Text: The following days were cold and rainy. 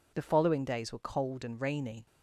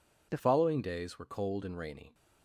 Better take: first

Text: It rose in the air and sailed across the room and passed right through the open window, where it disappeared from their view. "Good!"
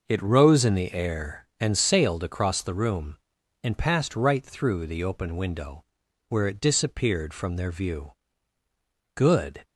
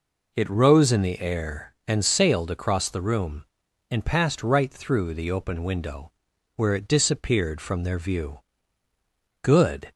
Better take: second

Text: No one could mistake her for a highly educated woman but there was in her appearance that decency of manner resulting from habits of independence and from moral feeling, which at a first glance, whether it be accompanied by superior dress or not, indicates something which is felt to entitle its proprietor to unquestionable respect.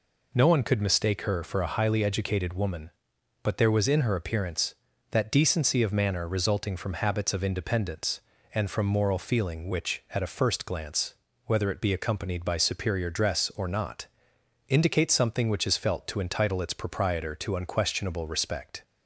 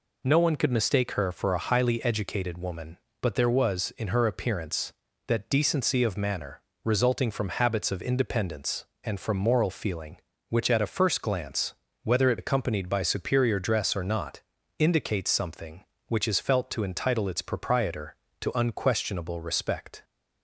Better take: first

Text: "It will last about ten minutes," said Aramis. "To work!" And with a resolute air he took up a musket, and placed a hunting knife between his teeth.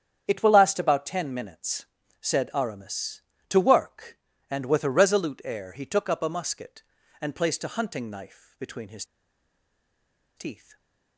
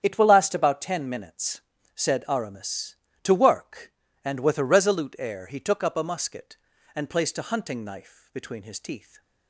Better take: second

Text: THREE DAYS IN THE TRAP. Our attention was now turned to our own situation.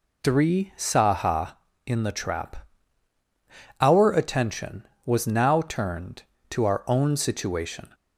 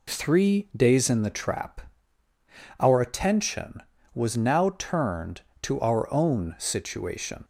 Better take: second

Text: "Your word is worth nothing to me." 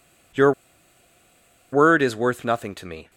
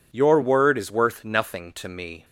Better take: second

